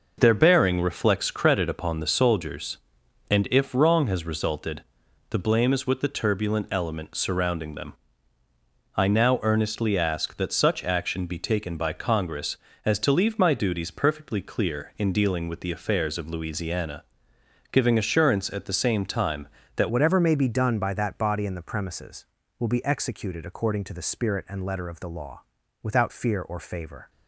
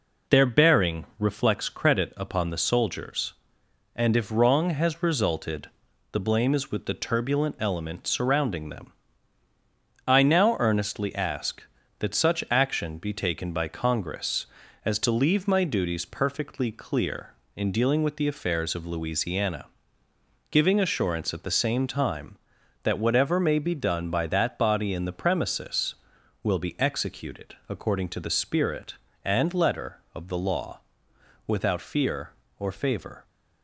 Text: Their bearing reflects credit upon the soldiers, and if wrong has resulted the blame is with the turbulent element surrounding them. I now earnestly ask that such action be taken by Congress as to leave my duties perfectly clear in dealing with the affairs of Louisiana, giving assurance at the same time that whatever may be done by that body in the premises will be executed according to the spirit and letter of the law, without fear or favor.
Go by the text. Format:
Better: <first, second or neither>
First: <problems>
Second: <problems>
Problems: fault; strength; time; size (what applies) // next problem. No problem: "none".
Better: second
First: pauses between "resulted" and "the"; noticeable; at 4.8 s; 0.48 s long // changes voice at "whatever"; from 19.8 s on; 7.2 s long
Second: pauses between "resulted" and "the"; at 5.6 s; 0.42 s long